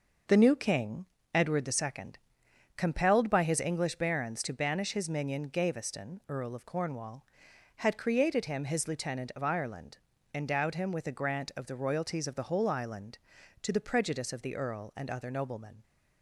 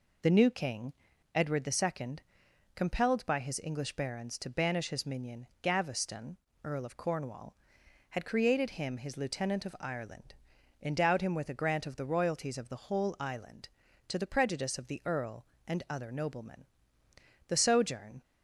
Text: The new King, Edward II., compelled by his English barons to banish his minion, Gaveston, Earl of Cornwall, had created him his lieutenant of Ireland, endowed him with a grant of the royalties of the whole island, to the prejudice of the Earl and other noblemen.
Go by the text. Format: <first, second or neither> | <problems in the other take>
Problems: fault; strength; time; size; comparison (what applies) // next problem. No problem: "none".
first | goes on to say "The sojourn"; noticeable; from 17.4 s on; 0.74 s long